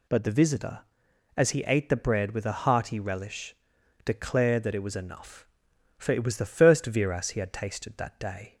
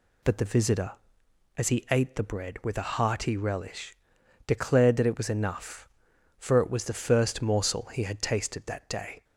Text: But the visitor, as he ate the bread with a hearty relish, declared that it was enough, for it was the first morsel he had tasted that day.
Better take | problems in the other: second | says "viras" for "morsel"; at 6.8 s

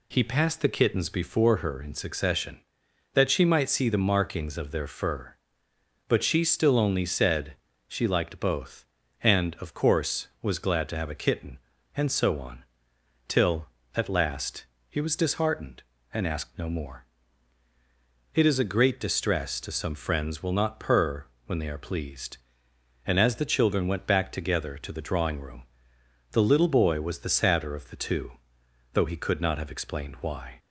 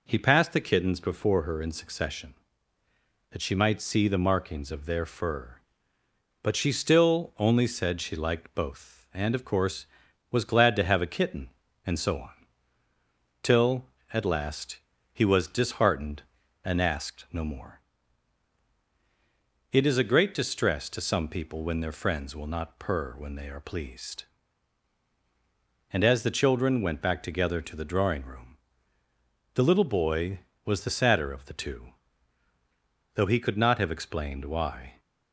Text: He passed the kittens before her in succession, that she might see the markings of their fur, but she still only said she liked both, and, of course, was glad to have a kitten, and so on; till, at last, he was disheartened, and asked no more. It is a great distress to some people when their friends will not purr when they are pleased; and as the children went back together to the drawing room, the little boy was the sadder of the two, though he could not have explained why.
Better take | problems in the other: second | pauses between "said" and "she"; slight; at 7.5 s; 0.34 s long // skips "people when their"; at 19.9 s // pauses between "purr" and "when"; slight; at 21.2 s; 0.22 s long

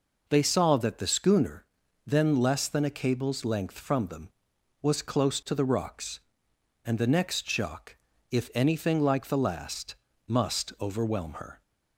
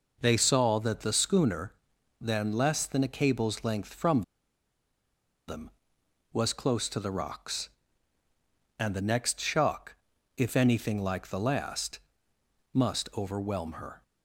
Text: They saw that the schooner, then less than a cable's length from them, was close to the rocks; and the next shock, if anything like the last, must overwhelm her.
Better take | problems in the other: first | pauses between "from" and "them"; strong; at 4.2 s; 1.2 s long

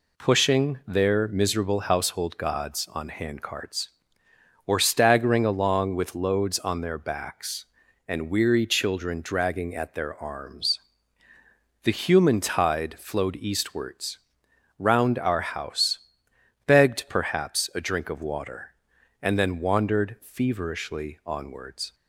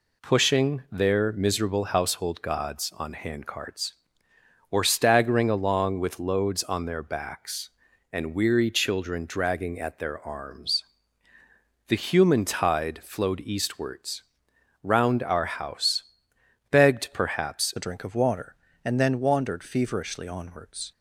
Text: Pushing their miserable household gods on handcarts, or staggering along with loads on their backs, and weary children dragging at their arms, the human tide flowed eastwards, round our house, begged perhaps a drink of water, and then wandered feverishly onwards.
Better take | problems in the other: first | changes voice at "a"; from 17.7 s on; 3.2 s long

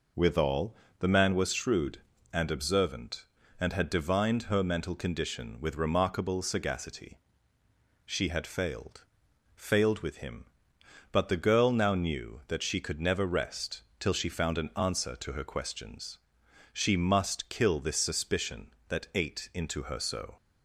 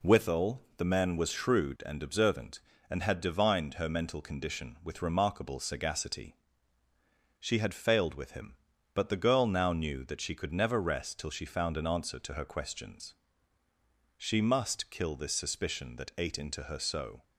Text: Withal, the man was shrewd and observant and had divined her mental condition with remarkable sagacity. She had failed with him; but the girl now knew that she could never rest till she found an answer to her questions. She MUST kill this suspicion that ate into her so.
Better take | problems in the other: second | says "failed" twice; at 9.5 s // pauses between "rest" and "till"; slight; at 13.8 s; 0.16 s long

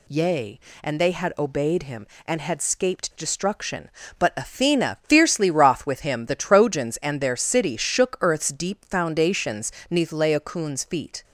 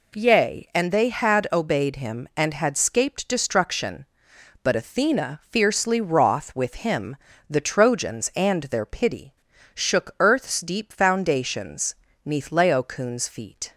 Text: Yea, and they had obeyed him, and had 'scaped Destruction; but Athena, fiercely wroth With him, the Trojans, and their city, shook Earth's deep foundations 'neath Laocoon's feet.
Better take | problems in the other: first | says "pity" for "city"; at 8.8 s // pauses between "foundations" and "neath"; slight; at 11.9 s; 0.30 s long; slight in the first

